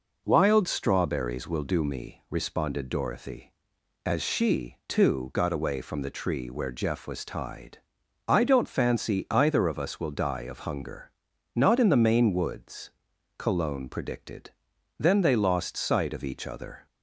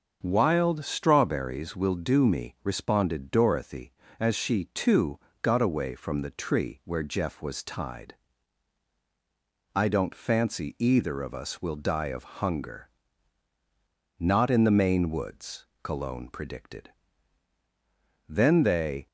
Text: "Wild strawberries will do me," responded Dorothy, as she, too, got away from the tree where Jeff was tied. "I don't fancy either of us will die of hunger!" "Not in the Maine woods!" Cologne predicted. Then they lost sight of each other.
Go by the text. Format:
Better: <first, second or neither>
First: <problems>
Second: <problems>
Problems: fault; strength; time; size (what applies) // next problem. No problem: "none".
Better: first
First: none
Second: starts louder than the rest; until 1.2 s; 6.5 dB // stops before "lost sight of each other"; at 19.0 s